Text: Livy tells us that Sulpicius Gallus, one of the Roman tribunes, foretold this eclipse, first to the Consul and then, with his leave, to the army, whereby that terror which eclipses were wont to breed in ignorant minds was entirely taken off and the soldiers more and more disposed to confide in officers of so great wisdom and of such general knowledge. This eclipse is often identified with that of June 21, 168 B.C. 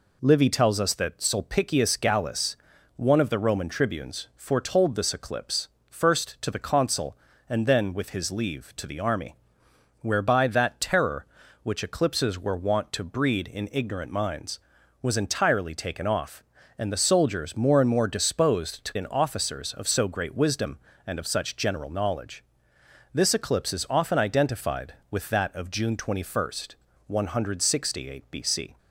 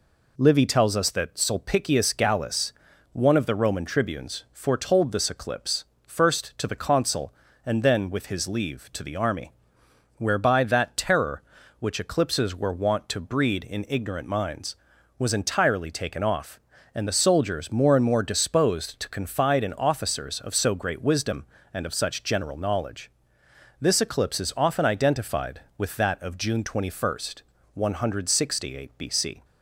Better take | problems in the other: second | skips "confide"; at 18.9 s

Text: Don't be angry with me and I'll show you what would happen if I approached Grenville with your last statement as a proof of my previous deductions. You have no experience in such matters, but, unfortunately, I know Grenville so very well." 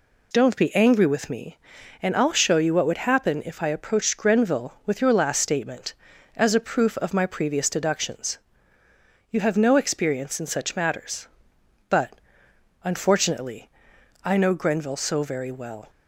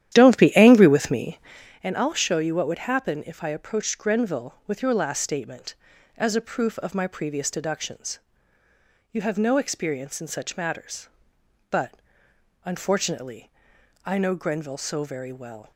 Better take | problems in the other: first | starts louder than the rest; strong; until 1.6 s; 11.5 dB

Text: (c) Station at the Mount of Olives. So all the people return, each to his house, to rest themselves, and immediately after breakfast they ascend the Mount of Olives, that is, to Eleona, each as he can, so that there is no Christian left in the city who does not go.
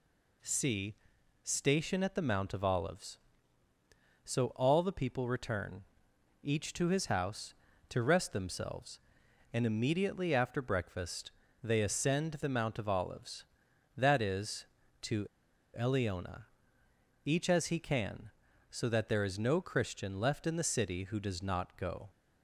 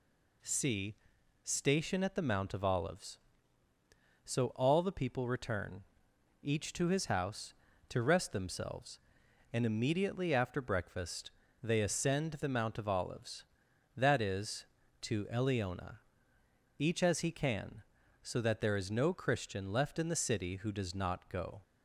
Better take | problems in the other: second | pauses between "breakfast" and "they"; slight; at 11.3 s; 0.30 s long; slight in the second // pauses between "to" and "Eleona"; noticeable; at 15.2 s; 0.48 s long

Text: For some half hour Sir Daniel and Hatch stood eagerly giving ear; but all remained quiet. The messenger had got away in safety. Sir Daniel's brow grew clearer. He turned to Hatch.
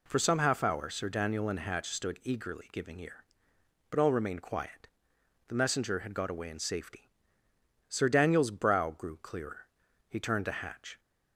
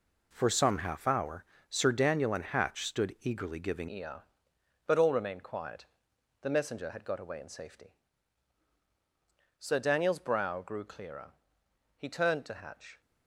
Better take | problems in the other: first | pauses between "hour" and "Sir"; slight; at 1.4 s; 0.24 s long // changes voice at "ear"; from 3.9 s on; 9.1 s long

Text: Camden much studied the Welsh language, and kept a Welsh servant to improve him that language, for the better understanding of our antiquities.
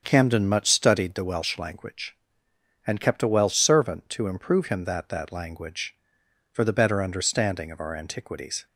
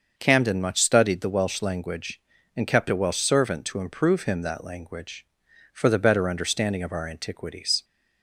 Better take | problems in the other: second | starts louder than the rest; until 1.0 s; 7 dB; also in the second // says "that" twice; at 5.0 s

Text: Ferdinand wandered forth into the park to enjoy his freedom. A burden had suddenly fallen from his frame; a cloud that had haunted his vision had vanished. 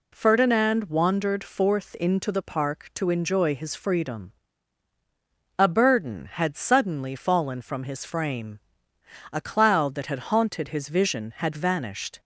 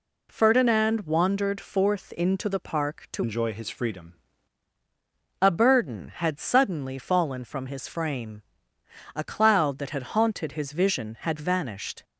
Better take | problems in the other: first | changes voice from "enjoy" to "freedom"; from 3.2 to 4.1 s; 0.9 s long

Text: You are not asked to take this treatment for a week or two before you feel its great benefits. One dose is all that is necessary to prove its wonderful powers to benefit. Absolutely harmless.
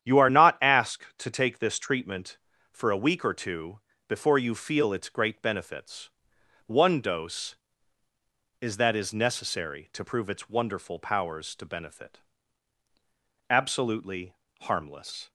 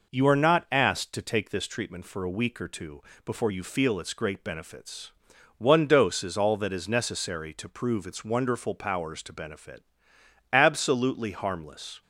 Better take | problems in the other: second | starts louder than the rest; strong; until 1.2 s; 9.5 dB // pauses between "two" and "before"; slight; at 3.8 s; 0.28 s long; slight in the second // skips "all"; at 8.7 s // pauses between "Absolutely" and "harmless"; slight; at 14.3 s; 0.26 s long

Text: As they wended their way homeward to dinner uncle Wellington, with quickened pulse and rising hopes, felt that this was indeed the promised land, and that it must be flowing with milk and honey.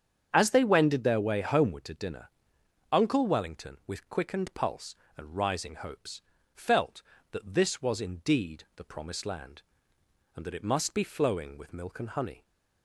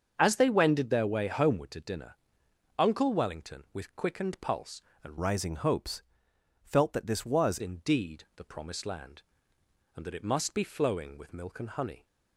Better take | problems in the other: first | starts louder than the rest; until 1.1 s; 7 dB; strong in the first // pauses between "dinner" and "uncle"; noticeable; at 2.1 s; 0.64 s long; noticeable in the first // changes voice from "rising" to "was"; from 5.2 to 7.5 s; 2.3 s long

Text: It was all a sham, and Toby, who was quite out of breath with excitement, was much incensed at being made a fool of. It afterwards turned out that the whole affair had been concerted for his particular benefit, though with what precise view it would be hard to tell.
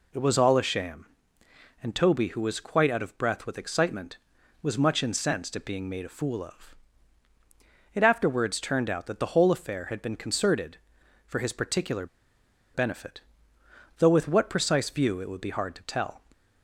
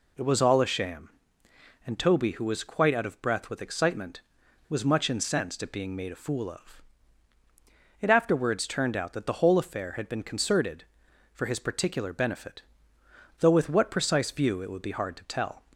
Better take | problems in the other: second | pauses between "particular" and "benefit"; noticeable; at 12.0 s; 0.67 s long

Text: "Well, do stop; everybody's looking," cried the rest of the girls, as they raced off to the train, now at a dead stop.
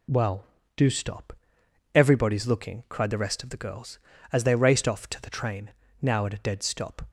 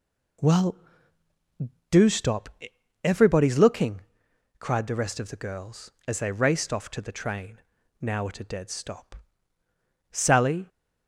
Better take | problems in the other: first | goes on to say "Sally"; from 10.1 s on; 0.56 s long

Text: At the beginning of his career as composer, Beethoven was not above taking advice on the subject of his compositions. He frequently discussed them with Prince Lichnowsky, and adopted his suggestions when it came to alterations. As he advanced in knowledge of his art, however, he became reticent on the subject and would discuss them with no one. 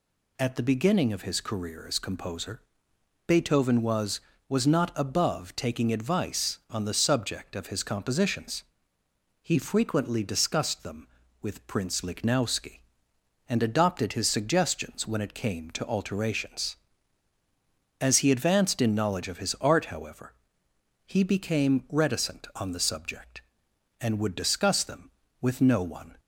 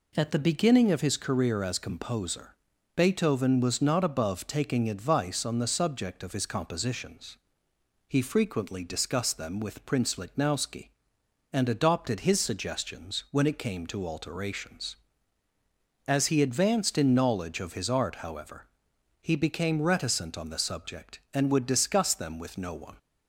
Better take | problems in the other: second | says "was" twice; at 4.4 s

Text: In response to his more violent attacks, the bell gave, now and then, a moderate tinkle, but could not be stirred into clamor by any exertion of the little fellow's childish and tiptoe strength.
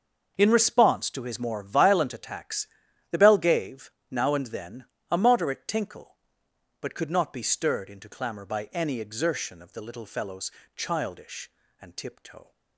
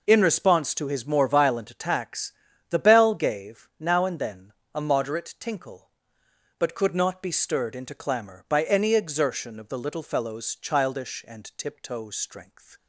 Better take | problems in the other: second | starts louder than the rest; until 1.3 s; 6 dB // pauses between "fellow's" and "childish"; slight; at 10.5 s; 0.24 s long // stops before "strength"; at 12.5 s

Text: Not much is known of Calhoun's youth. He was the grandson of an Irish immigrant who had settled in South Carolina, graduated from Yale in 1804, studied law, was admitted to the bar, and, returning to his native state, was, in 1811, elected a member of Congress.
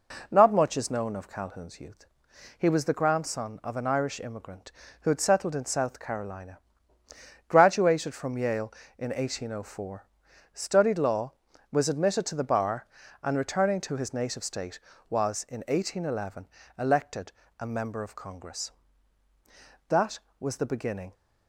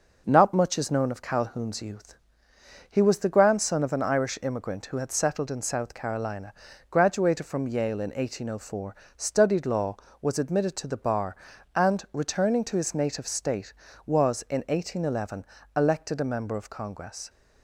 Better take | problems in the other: second | pauses between "elected" and "a"; slight; at 17.3 s; 0.28 s long // goes on to say "That was the beginning"; noticeable; from 19.8 s on; 1.2 s long

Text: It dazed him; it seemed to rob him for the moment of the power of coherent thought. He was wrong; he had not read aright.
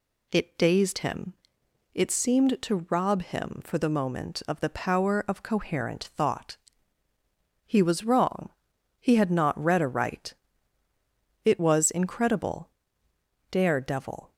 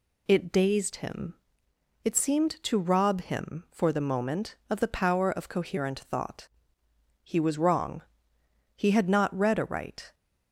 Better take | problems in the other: second | goes on to say "It was incredible dare devil"; strong; from 11.4 s on; 2.8 s long

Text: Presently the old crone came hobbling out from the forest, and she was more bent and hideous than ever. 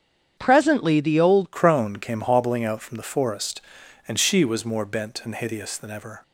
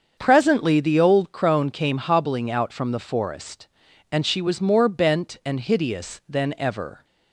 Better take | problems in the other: second | starts louder than the rest; strong; until 1.4 s; 8 dB; also in the second // changes voice at "crone"; from 1.5 s on; 4.7 s long

